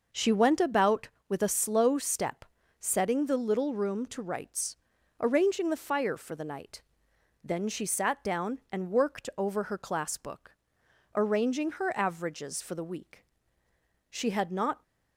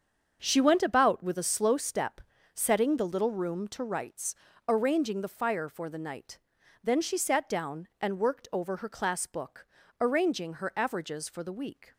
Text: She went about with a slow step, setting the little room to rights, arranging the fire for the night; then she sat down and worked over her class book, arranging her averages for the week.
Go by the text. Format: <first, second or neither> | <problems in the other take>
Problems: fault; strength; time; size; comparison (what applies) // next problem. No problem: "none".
second | starts louder than the rest; noticeable; until 1.3 s; 6 dB; also in the second // goes on to say "She had not"; noticeable; from 14.1 s on; 0.72 s long